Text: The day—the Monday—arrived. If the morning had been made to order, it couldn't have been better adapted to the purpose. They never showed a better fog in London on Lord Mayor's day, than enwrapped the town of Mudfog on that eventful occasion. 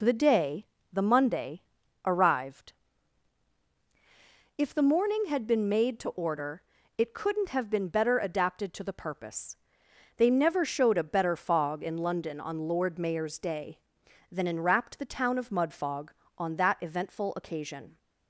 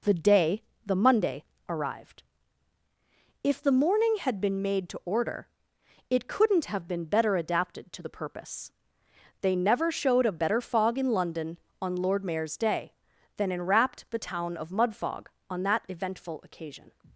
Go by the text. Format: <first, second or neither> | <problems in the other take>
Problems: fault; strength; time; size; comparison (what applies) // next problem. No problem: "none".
neither | none